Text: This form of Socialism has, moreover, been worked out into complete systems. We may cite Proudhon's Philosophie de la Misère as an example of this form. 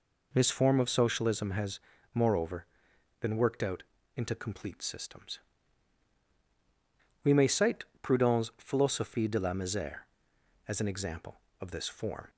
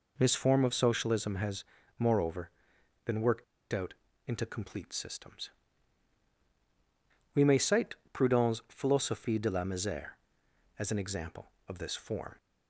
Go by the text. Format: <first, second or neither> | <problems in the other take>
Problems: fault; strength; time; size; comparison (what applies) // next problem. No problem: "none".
first | pauses between "worked" and "out"; slight; at 3.4 s; 0.28 s long // pauses between "out" and "into"; slight; at 3.9 s; 0.34 s long; slight in the first // pauses between "cite" and "Proudhon's"; slight; at 7.9 s; 0.18 s long; slight in the first